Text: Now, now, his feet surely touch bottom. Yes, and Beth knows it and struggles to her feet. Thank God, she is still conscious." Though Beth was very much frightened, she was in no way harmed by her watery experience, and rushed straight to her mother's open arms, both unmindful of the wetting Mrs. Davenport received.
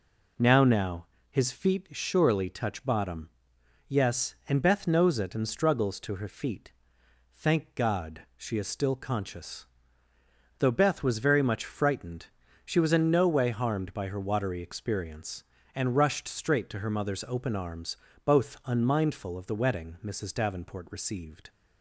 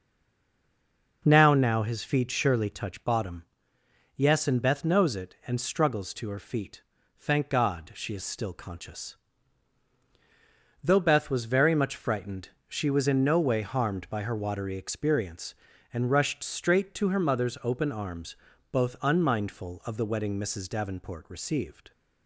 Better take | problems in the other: first | stays silent before the first word; noticeable; until 1.2 s; 1.2 s long

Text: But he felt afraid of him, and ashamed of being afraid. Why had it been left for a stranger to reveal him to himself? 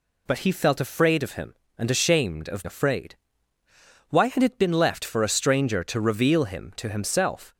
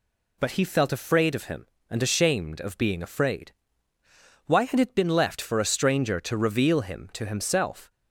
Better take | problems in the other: second | skips "being"; at 2.6 s

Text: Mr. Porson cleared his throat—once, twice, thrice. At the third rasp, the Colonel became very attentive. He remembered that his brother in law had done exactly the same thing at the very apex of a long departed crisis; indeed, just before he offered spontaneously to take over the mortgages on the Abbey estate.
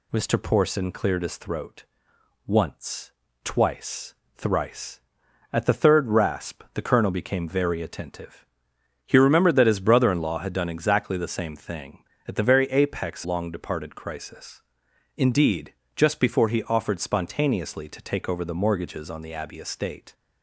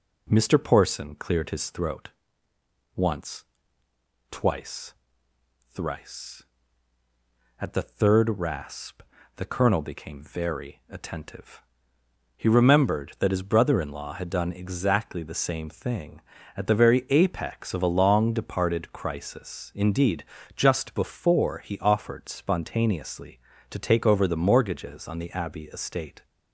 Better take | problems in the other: second | skips "of a"; at 13.2 s

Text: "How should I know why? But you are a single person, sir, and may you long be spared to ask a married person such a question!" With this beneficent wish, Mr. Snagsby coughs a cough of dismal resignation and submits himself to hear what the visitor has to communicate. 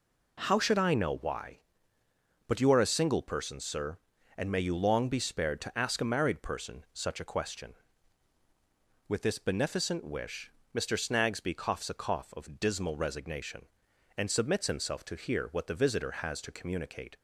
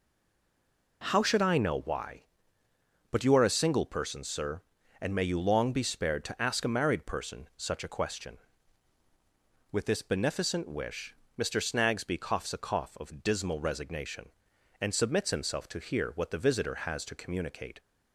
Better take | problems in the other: first | stays silent before the first word; until 1.0 s; 1.0 s long

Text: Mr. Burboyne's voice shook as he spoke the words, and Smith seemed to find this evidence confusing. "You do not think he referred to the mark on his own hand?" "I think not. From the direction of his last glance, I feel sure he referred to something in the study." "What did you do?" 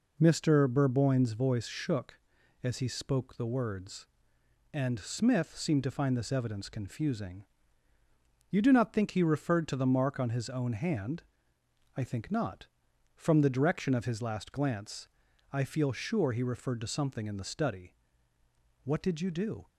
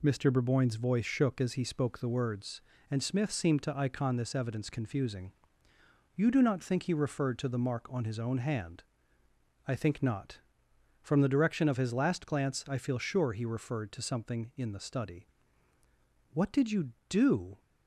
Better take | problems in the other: first | says "icon" for "find"; at 3.7 s

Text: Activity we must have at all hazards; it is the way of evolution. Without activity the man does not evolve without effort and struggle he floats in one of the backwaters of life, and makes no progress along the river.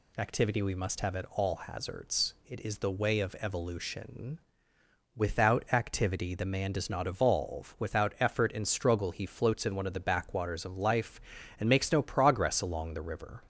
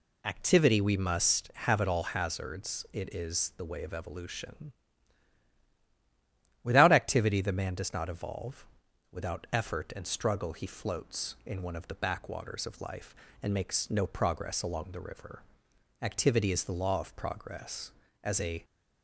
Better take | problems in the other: first | pauses between "evolve" and "without"; noticeable; at 8.6 s; 0.46 s long // goes on to say "Activity is the law of progress as a"; strong; from 16.0 s on; 2.6 s long

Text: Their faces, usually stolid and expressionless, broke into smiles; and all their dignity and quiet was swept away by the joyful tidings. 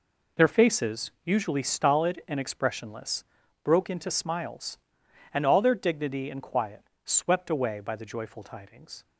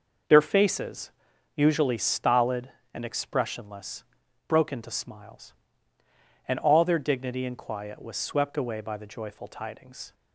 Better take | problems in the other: second | skips "was"; at 6.9 s

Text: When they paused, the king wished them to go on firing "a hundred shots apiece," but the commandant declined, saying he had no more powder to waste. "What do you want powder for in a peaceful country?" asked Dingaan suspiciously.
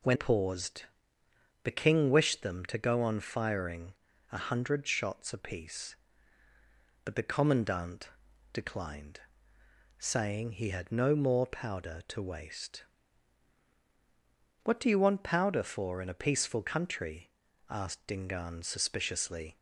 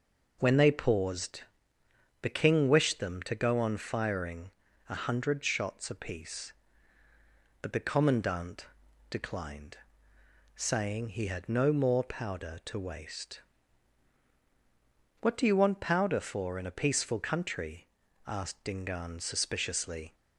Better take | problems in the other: second | skips "they"; at 0.1 s // pauses between "firing" and "a"; slight; at 3.9 s; 0.36 s long; slight in the second // pauses between "commandant" and "declined"; at 8.1 s; 0.42 s long; also in the second

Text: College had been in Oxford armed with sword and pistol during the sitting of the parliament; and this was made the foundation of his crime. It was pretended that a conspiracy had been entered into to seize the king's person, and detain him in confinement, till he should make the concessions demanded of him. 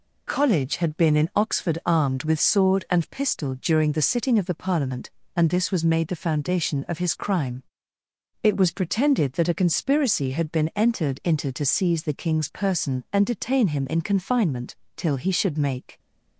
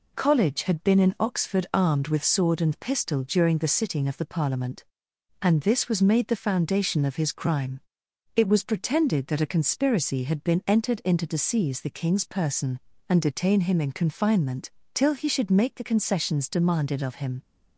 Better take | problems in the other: second | stops before "the concessions demanded of him"; at 15.9 s

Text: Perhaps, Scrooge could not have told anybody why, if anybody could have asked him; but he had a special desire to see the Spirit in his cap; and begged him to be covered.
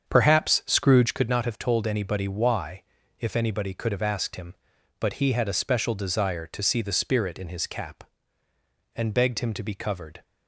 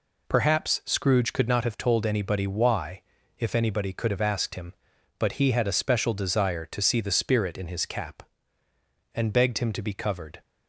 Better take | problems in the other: second | starts louder than the rest; strong; until 1.2 s; 7.5 dB

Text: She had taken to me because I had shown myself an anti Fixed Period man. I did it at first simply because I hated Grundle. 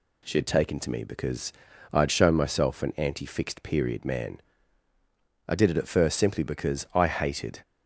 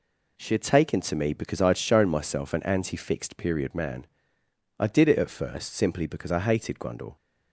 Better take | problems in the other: second | pauses between "because" and "I"; at 1.5 s; 0.40 s long // stops before "Grundle"; at 7.6 s

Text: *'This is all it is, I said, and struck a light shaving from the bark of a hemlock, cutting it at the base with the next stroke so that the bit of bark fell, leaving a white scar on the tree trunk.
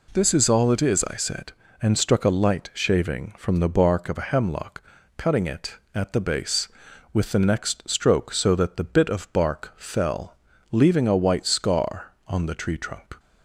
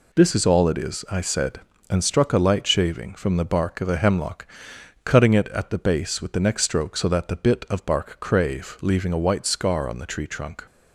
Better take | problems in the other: first | says "crave" for "fell"; at 8.1 s

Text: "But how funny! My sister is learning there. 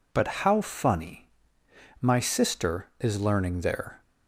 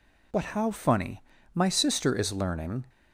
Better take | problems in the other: first | stops before "there"; at 2.8 s

